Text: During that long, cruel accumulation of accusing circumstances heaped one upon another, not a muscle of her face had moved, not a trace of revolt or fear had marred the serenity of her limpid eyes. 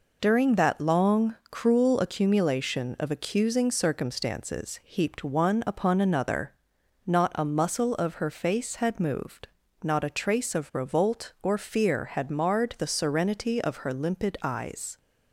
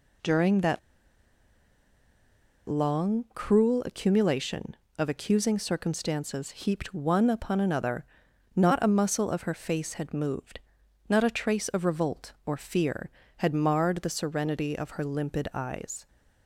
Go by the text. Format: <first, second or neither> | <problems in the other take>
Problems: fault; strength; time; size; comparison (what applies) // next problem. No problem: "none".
first | pauses between "that" and "long"; strong; at 0.7 s; 1.8 s long